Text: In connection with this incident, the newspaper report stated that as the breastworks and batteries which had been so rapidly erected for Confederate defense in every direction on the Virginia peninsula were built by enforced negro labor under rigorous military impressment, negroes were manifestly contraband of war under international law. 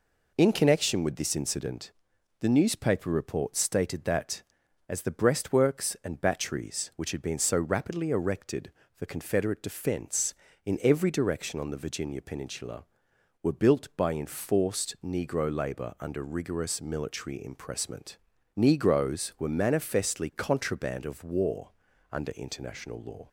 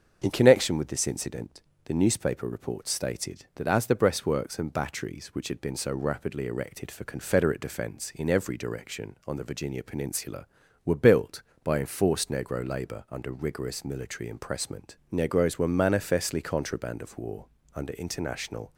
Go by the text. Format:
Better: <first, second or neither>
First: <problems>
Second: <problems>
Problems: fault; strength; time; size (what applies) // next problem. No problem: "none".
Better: first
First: pauses between "war" and "under"; at 21.6 s; 0.40 s long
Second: starts louder than the rest; until 1.2 s; 7 dB // pauses between "war" and "under"; slight; at 17.4 s; 0.30 s long // stops before "law"; at 18.7 s